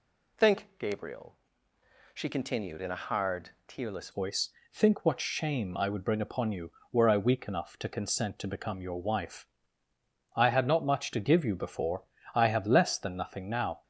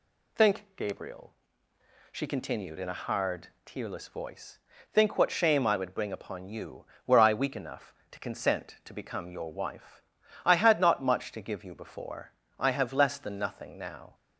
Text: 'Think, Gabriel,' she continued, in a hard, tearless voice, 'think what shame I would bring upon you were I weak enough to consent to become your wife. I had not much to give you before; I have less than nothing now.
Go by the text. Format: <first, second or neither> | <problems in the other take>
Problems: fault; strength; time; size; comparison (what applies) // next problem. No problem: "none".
second | changes voice at "voice"; from 4.1 s on; 9.7 s long